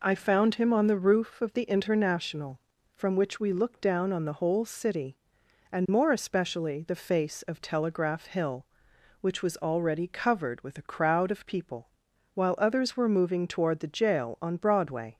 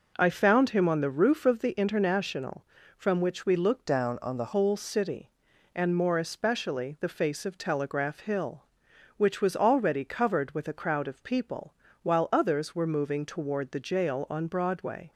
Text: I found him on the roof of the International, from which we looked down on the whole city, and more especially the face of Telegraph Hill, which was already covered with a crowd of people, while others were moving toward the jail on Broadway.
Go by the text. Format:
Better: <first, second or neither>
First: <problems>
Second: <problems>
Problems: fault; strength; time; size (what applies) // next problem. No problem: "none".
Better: first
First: none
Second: changes voice from "down" to "the"; from 3.8 to 4.5 s; 0.7 s long